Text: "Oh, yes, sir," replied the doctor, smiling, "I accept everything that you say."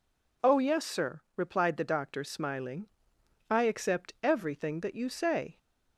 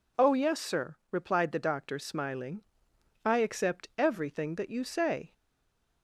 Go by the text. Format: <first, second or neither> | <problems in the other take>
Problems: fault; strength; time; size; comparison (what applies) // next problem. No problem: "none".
first | stays silent after the last word; slight; from 5.3 s on; 0.7 s long